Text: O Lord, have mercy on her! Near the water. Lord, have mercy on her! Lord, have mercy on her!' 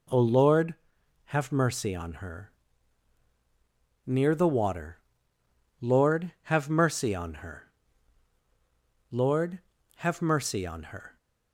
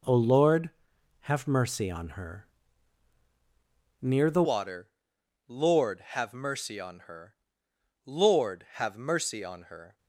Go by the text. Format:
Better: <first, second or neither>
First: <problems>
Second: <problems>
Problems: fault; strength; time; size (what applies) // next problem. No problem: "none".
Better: first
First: none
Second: changes voice at "water"; from 4.4 s on; 5.5 s long